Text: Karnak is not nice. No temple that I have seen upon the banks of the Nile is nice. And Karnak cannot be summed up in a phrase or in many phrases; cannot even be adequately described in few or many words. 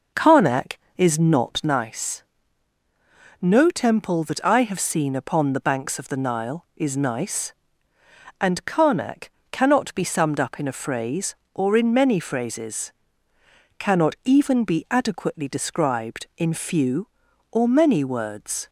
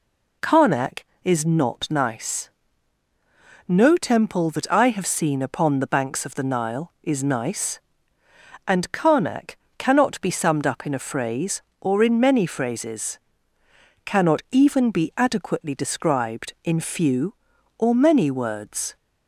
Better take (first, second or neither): second